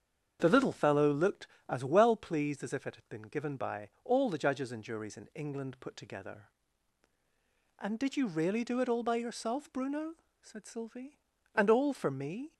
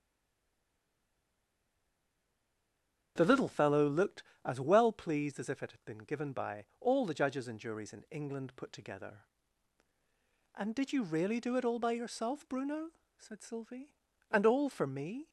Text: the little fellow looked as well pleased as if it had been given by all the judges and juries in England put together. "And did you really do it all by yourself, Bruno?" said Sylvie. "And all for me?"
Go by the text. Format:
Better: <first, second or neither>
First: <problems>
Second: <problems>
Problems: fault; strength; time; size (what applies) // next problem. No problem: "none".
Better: first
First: starts louder than the rest; strong; until 1.4 s; 7.5 dB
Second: stays silent before the first word; strong; until 3.1 s; 3.1 s long // starts louder than the rest; strong; until 4.1 s; 7.5 dB